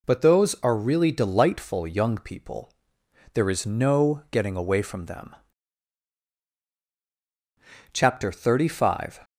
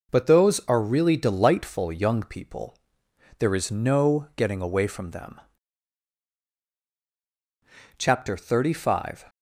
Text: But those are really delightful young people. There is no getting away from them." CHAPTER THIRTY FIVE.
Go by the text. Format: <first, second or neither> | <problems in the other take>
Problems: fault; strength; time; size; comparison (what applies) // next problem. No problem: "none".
first | gets quieter; noticeable; throughout; 4.5 dB